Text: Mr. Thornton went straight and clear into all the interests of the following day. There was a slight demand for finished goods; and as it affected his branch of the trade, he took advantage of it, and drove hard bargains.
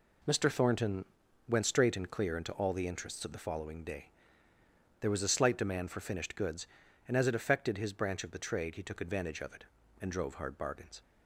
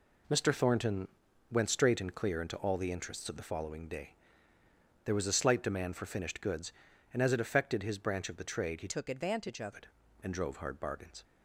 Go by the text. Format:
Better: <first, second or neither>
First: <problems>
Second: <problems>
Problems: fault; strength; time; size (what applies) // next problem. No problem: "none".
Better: first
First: pauses between "Thornton" and "went"; at 1.0 s; 0.44 s long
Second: pauses between "Thornton" and "went"; at 1.0 s; 0.44 s long // changes voice from "took" to "of"; from 8.8 to 9.7 s; 0.9 s long